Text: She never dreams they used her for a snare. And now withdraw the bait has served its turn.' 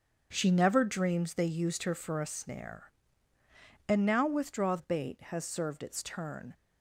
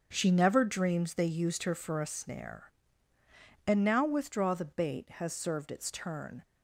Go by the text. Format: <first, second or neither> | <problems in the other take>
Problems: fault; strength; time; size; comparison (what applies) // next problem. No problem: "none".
second | starts louder than the rest; until 1.3 s; 7 dB; also in the second // skips "the"; at 4.7 s